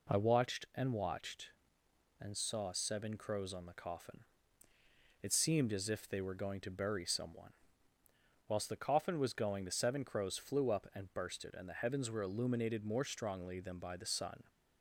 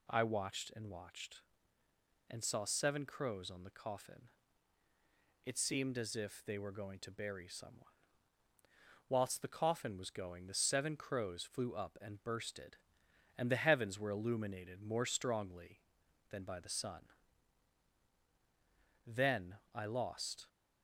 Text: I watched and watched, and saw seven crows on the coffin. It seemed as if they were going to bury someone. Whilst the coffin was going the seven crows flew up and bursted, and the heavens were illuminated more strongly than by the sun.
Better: first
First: none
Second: goes on to say "Then I lost"; from 19.0 s on; 1.4 s long

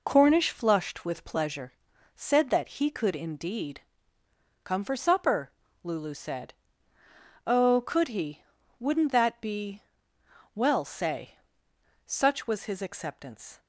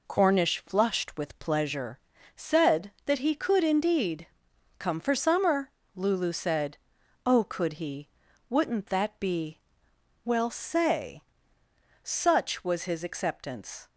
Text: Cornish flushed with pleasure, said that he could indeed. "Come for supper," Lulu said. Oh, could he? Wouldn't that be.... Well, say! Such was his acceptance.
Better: first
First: none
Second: says "summer" for "supper"; at 5.1 s

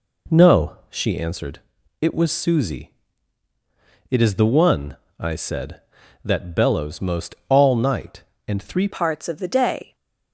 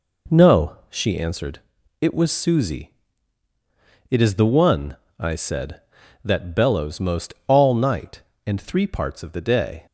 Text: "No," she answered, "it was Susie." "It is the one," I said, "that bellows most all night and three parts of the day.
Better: second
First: changes voice at "parts"; from 8.9 s on; 1.0 s long // stays silent after the last word; slight; from 9.8 s on; 0.5 s long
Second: none

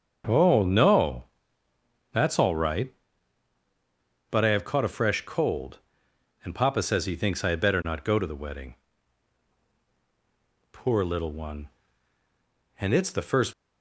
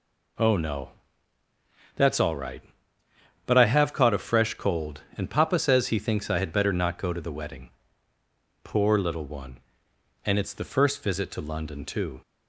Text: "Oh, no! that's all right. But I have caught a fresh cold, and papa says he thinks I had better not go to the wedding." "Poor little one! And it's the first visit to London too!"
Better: second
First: starts louder than the rest; until 2.1 s; 6.5 dB // stops before "visit to London too"; at 13.5 s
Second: none

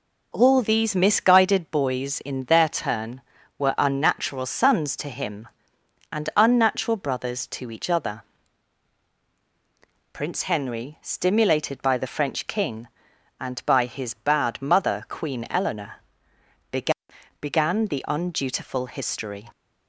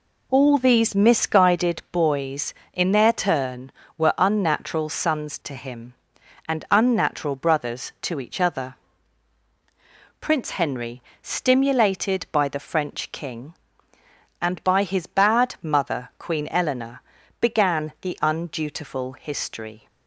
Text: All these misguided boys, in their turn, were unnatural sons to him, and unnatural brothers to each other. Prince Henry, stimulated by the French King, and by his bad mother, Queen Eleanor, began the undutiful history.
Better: second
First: says "began" twice; at 17.8 s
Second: none

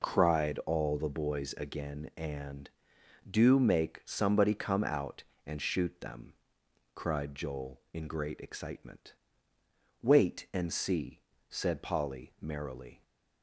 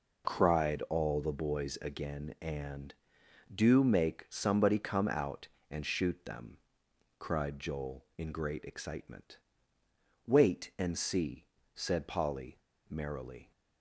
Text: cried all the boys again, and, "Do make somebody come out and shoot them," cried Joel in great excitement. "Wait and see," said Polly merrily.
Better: first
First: none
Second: pauses between "Polly" and "merrily"; slight; at 12.5 s; 0.31 s long

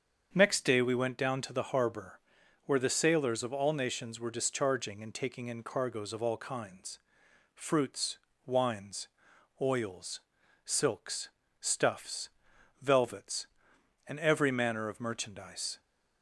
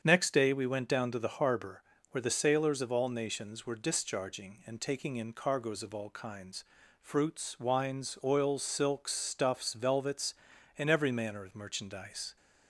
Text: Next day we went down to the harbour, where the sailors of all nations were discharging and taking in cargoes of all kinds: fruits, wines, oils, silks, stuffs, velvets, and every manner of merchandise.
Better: neither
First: starts louder than the rest; strong; until 1.3 s; 7 dB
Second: starts louder than the rest; strong; until 1.0 s; 7.5 dB

